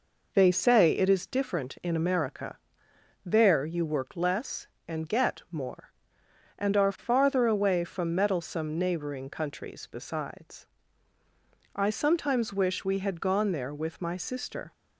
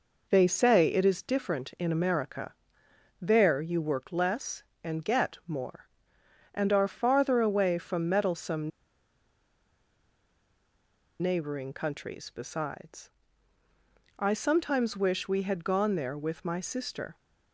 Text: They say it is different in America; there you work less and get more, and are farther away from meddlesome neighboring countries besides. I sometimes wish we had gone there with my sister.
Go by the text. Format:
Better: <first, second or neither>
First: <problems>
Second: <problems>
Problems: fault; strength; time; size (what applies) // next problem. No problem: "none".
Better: first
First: none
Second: pauses between "meddlesome" and "neighboring"; strong; at 8.7 s; 2.5 s long